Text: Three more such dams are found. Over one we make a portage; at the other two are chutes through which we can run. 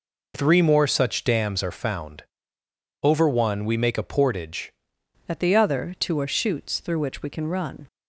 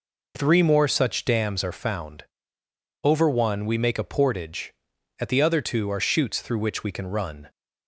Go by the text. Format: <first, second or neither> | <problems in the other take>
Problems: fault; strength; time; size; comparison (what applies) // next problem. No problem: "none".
second | changes voice at "at"; from 5.2 s on; 2.6 s long